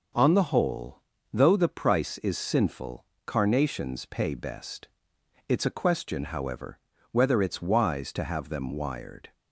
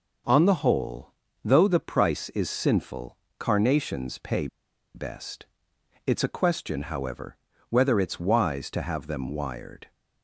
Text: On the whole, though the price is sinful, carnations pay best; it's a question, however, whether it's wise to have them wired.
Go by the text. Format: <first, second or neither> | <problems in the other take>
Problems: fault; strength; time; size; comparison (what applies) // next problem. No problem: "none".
first | pauses between "pay" and "best"; noticeable; at 4.4 s; 0.47 s long